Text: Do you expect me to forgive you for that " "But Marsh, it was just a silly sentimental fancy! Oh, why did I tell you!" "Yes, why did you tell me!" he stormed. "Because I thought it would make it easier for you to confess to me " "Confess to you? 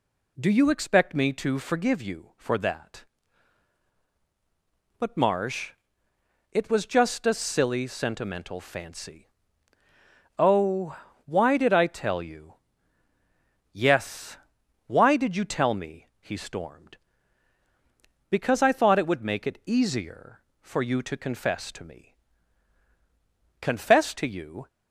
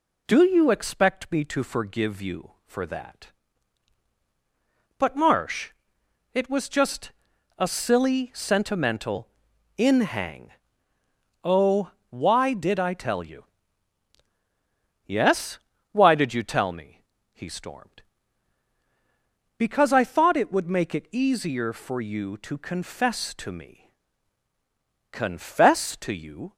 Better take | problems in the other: first | pauses between "just" and "a"; noticeable; at 7.1 s; 0.48 s long // says "inhang" for "fancy"; at 9.7 s

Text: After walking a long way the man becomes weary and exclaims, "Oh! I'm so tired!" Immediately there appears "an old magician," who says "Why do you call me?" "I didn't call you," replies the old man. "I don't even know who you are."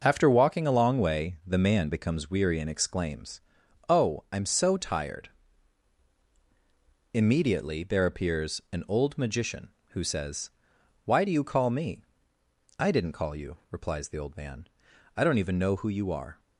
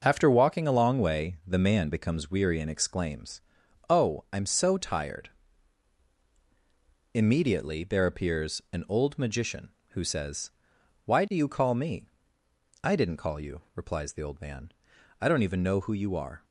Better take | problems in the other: neither | pauses between "says" and "Why"; noticeable; the same in both

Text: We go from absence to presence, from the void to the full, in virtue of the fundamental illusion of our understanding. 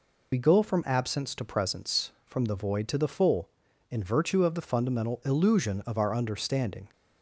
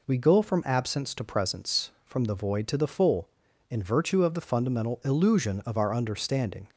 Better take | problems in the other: second | loses the start of "We"; at 0.3 s; 60 ms

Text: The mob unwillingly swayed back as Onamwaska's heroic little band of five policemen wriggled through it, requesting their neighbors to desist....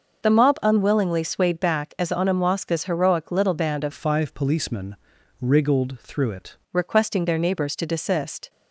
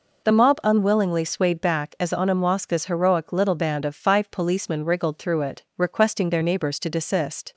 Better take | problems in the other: second | changes voice from "five" to "it"; from 3.9 to 6.5 s; 2.6 s long // pauses between "policemen" and "wriggled"; at 4.9 s; 0.44 s long

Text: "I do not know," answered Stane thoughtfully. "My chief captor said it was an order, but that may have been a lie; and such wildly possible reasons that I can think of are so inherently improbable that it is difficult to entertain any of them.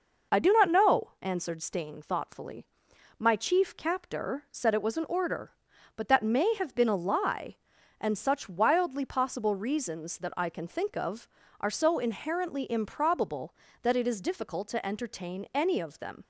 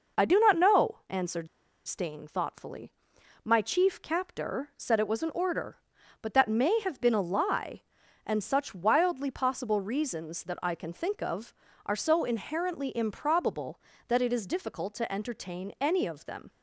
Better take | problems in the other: first | pauses between "answered" and "Stane"; at 1.4 s; 0.39 s long

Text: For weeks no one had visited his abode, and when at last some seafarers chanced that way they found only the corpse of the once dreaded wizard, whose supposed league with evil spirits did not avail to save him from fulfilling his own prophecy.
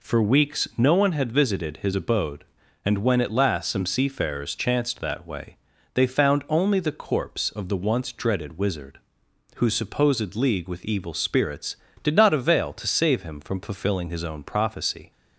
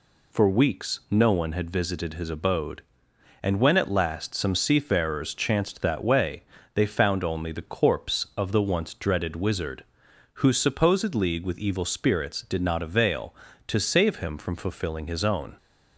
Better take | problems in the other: first | pauses between "way" and "they"; slight; at 6.4 s; 0.30 s long; slight in the first // stops before "prophecy"; at 15.5 s

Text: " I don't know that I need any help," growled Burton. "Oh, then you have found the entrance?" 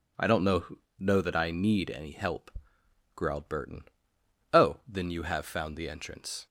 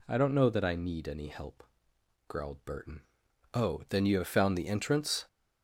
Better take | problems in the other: second | says "know" twice; at 0.9 s

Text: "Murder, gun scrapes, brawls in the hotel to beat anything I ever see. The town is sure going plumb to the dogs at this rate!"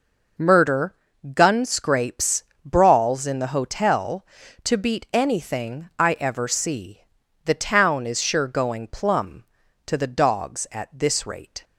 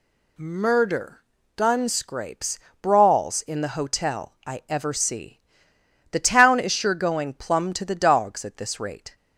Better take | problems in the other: first | skips "to beat anything"; at 4.4 s

